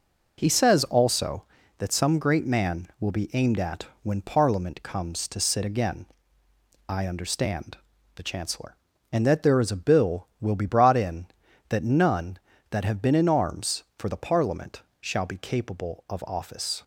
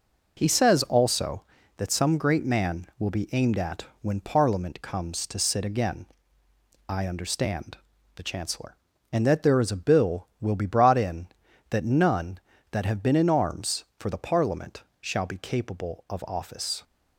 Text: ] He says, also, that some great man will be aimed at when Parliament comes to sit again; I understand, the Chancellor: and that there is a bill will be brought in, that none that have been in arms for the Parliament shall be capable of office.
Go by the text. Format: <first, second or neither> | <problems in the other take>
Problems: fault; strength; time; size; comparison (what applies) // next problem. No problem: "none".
neither | pauses between "at" and "when"; slight; the same in both // pauses between "Parliament" and "shall"; slight; the same in both